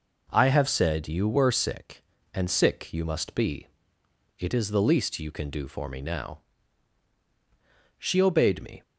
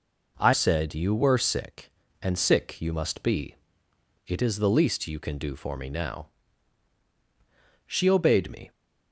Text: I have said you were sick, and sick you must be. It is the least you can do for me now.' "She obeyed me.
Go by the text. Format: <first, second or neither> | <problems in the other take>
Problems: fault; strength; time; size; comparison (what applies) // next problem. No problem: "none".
first | skips "have"; at 0.5 s